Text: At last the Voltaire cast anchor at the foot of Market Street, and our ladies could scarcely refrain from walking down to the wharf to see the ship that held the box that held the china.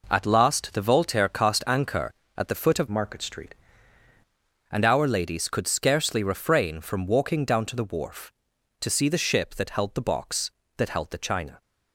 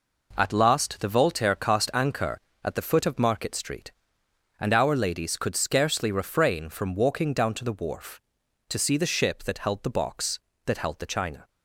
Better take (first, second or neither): second